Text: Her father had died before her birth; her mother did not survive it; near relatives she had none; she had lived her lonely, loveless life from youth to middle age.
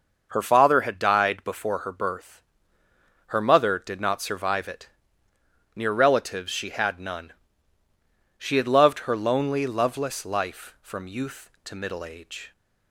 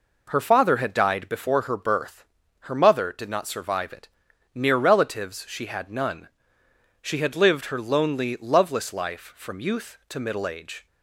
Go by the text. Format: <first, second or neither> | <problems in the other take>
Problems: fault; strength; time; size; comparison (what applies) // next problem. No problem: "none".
second | starts louder than the rest; noticeable; until 1.3 s; 6 dB // says "loved" for "lived"; at 8.6 s